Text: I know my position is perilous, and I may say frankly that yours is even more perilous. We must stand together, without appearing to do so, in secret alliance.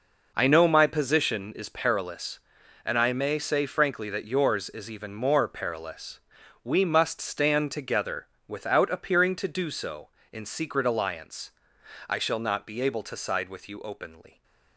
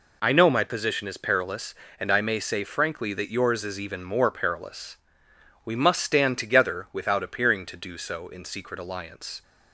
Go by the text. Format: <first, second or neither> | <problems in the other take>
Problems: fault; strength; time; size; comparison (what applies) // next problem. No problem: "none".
second | goes on to say "I shall not be able to side with you openly"; strong; from 12.0 s on; 2.3 s long